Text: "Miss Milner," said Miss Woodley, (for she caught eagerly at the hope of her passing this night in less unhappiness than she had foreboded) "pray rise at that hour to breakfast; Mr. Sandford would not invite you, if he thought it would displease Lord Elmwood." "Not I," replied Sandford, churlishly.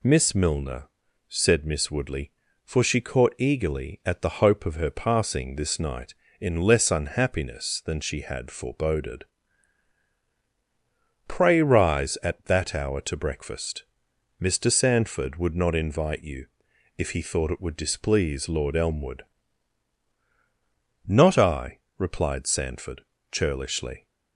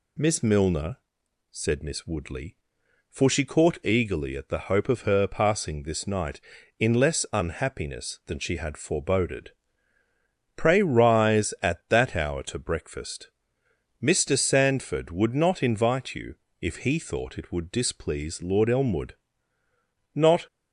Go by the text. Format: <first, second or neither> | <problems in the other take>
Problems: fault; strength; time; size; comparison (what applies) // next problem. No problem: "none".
first | stops before "I replied Sandford churlishly"; at 20.4 s